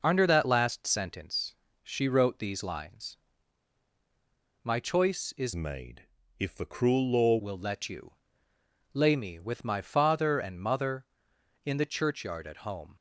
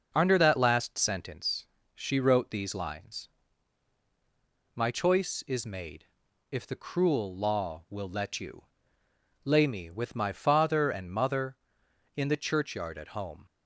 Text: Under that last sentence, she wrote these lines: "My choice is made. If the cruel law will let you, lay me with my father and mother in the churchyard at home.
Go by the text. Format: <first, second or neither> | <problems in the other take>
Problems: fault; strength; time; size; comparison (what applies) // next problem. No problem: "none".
second | changes voice from "made" to "law"; from 5.5 to 7.3 s; 1.8 s long